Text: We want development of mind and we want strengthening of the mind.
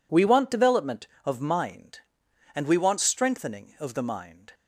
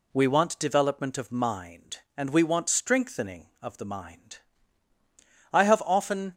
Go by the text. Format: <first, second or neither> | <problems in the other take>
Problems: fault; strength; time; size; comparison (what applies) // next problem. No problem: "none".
first | goes on to say "I have often"; noticeable; from 5.5 s on; 0.82 s long